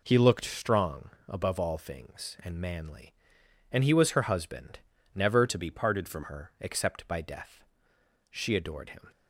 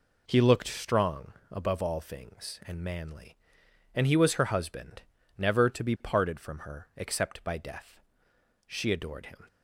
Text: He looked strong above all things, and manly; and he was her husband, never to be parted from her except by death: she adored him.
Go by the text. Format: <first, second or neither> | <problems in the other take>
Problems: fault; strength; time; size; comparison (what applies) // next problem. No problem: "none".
second | pauses between "strong" and "above"; slight; at 1.1 s; 0.18 s long; slight in the second // changes voice from "to" to "from"; from 5.4 to 6.2 s; 0.8 s long